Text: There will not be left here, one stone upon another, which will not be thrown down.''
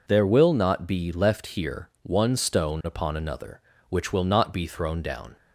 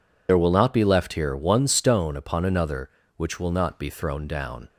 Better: first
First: none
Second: loses the start of "There"; at 0.2 s; 60 ms

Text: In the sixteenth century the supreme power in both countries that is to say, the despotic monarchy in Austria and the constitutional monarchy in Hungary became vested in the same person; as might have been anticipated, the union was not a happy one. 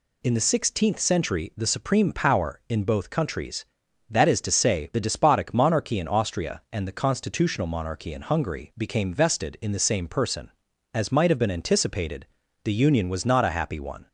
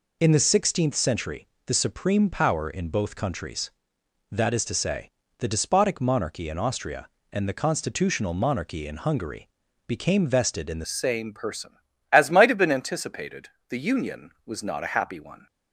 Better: first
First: none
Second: pauses between "century" and "the"; slight; at 1.4 s; 0.20 s long // pauses between "Hungary" and "became"; at 9.4 s; 0.38 s long // changes voice at "same"; from 10.8 s on; 4.6 s long

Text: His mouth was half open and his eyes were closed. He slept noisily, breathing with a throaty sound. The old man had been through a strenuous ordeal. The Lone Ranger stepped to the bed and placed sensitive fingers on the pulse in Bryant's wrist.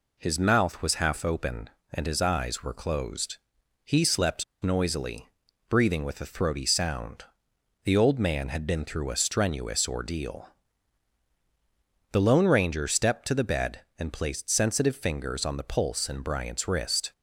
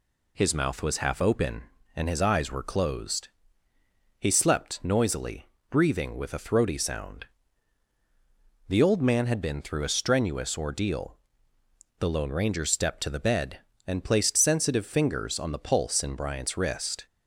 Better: second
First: pauses between "slept" and "noisily"; slight; at 4.4 s; 0.17 s long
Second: none

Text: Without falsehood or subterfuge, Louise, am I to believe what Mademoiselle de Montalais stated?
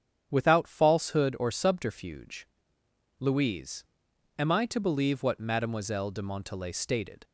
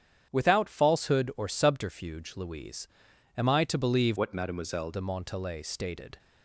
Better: first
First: starts louder than the rest; strong; until 1.3 s; 9 dB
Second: starts louder than the rest; strong; until 1.3 s; 9 dB // changes voice from "what" to "Mademoiselle"; from 4.1 to 4.9 s; 0.8 s long

